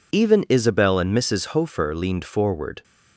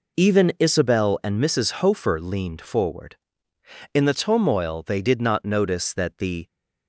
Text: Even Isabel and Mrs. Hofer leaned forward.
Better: first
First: none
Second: goes on to say "In the turmoil they did not notice that the"; strong; from 3.9 s on; 2.5 s long

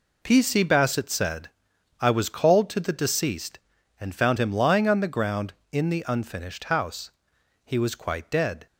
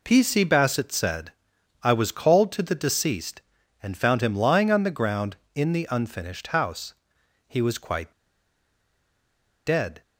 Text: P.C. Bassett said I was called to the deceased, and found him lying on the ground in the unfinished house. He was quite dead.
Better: first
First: pauses between "said" and "I"; noticeable; at 1.4 s; 0.50 s long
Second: pauses between "said" and "I"; noticeable; at 1.3 s; 0.50 s long // pauses between "quite" and "dead"; strong; at 8.1 s; 1.5 s long

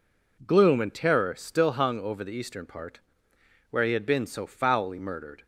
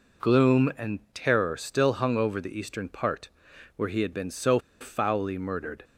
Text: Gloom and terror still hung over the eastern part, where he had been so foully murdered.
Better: first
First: none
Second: pauses between "and" and "terror"; slight; at 0.9 s; 0.16 s long // pauses between "so" and "foully"; slight; at 4.5 s; 0.21 s long

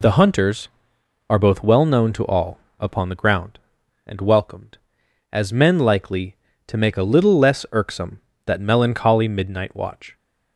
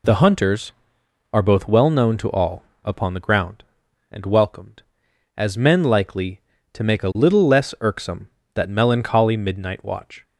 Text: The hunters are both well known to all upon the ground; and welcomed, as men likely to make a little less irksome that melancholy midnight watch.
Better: neither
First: pauses between "all" and "upon"; slight; at 2.5 s; 0.22 s long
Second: pauses between "all" and "upon"; slight; at 2.6 s; 0.22 s long

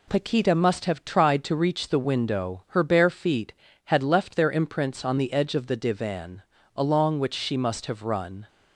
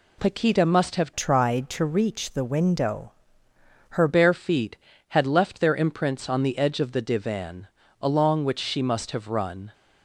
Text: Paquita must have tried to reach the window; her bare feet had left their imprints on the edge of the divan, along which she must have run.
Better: first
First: none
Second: changes voice from "tried" to "her"; from 1.1 to 4.0 s; 2.9 s long

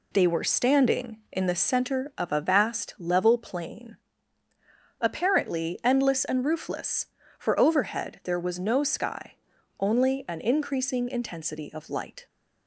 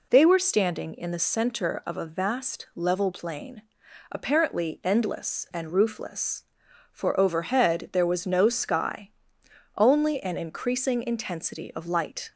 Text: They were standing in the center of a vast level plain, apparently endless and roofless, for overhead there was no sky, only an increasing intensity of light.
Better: neither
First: none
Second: none

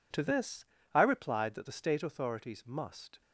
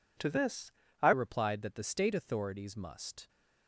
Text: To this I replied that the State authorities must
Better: first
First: pauses between "this" and "I"; slight; at 0.6 s; 0.26 s long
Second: pauses between "this" and "I"; slight; at 0.7 s; 0.28 s long // changes voice at "replied"; from 1.1 s on; 2.1 s long

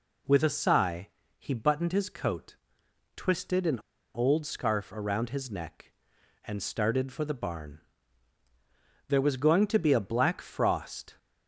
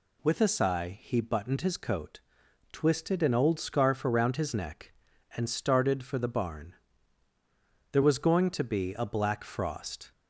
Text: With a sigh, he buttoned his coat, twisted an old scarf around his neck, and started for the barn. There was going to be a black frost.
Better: second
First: pauses between "an" and "old"; slight; at 3.7 s; 0.35 s long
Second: none

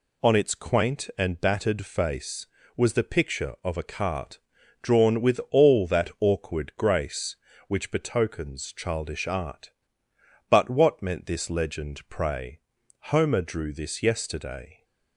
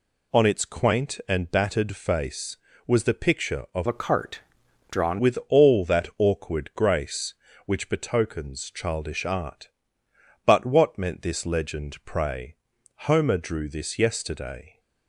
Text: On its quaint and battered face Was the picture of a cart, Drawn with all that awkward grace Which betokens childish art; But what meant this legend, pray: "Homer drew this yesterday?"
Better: first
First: none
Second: changes voice from "a" to "Drawn"; from 3.8 to 5.1 s; 1.3 s long

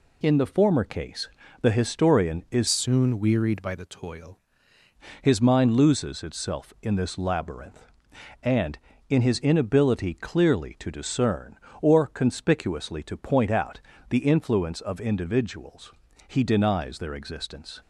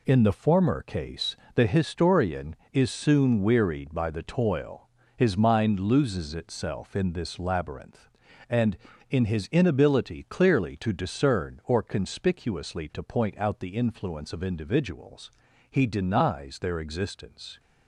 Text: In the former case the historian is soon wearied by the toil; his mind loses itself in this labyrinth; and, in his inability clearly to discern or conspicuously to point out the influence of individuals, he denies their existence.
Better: second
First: pauses between "case" and "the"; slight; at 1.2 s; 0.34 s long // changes voice from "soon" to "toil"; from 2.6 to 4.3 s; 1.7 s long // pauses between "out" and "the"; slight; at 13.8 s; 0.30 s long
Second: pauses between "case" and "the"; slight; at 1.3 s; 0.18 s long

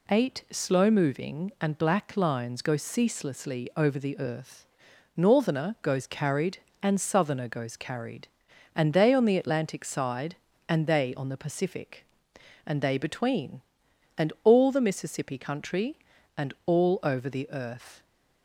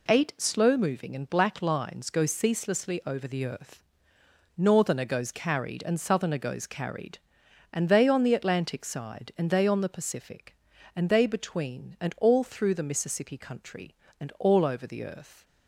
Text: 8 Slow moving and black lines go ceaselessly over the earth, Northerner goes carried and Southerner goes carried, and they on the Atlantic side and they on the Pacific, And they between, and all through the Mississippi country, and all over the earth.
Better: second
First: skips "through"; at 14.6 s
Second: none

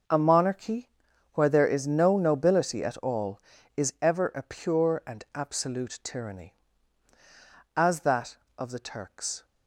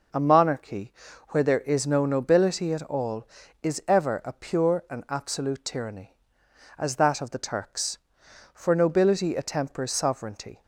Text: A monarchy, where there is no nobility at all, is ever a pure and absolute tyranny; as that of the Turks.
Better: first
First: none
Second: goes on to say "For nobility attempers sovereignty"; strong; from 8.5 s on; 2.1 s long

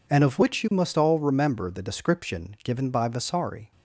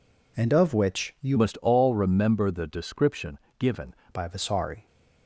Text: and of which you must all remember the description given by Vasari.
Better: first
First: none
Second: changes voice from "must" to "given"; from 1.3 to 3.9 s; 2.6 s long // pauses between "description" and "given"; slight; at 3.3 s; 0.22 s long

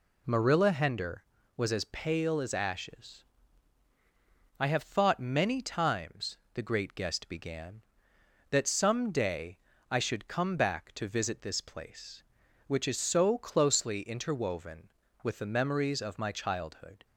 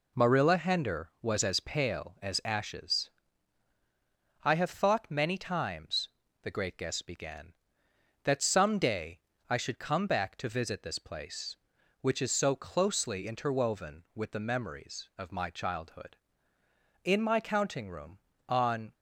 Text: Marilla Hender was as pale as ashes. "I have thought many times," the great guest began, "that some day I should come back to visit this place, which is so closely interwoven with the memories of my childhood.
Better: first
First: pauses between "day" and "I"; slight; at 9.5 s; 0.32 s long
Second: pauses between "day" and "I"; slight; at 9.1 s; 0.32 s long // goes on to say "In my counting room on"; strong; from 17.0 s on; 1.9 s long

